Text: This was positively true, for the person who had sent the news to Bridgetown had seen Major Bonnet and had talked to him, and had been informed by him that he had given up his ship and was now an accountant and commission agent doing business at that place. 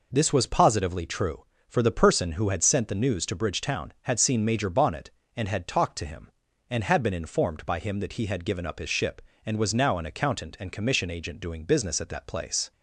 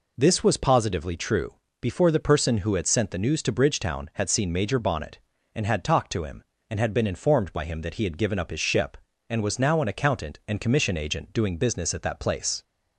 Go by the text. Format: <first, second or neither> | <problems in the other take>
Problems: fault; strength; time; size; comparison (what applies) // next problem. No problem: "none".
first | says "before" for "for"; at 1.8 s